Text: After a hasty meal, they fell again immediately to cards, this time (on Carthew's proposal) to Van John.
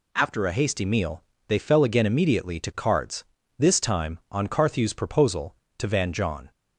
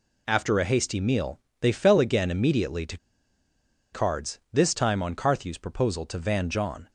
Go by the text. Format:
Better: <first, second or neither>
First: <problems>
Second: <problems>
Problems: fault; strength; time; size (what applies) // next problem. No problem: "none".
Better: first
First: none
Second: pauses between "to" and "cards"; noticeable; at 2.9 s; 0.95 s long